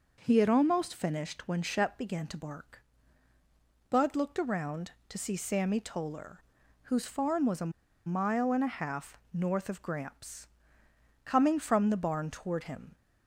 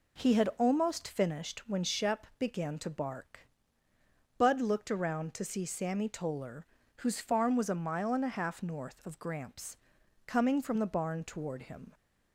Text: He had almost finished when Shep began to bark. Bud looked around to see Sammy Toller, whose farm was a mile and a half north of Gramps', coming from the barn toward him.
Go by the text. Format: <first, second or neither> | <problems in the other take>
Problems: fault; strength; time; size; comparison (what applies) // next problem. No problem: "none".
second | pauses between "a" and "mile"; at 7.7 s; 0.36 s long